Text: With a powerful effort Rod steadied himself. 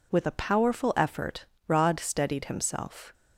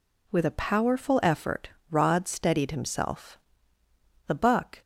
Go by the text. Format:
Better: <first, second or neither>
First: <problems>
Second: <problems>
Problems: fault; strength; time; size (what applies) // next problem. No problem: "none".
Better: first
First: pauses between "effort" and "Rod"; slight; at 1.4 s; 0.22 s long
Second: pauses between "effort" and "Rod"; slight; at 1.6 s; 0.20 s long // goes on to say "The buck"; from 4.2 s on; 0.54 s long